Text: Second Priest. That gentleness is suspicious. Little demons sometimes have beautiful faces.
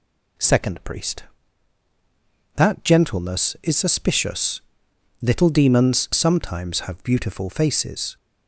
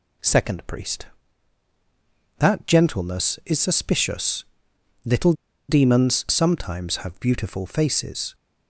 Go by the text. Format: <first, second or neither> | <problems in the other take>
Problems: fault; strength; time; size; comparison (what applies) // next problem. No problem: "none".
first | pauses between "Little" and "demons"; slight; at 5.3 s; 0.35 s long